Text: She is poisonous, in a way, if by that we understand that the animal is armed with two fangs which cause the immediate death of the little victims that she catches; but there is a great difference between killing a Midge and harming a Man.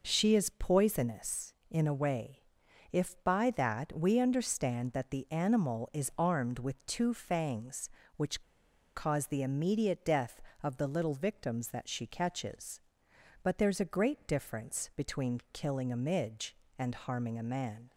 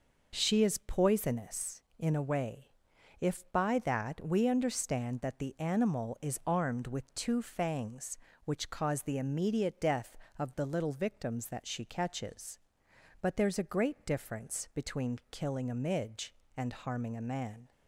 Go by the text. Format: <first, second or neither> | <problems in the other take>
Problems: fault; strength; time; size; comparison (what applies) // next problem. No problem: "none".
second | pauses between "which" and "cause"; noticeable; at 8.4 s; 0.53 s long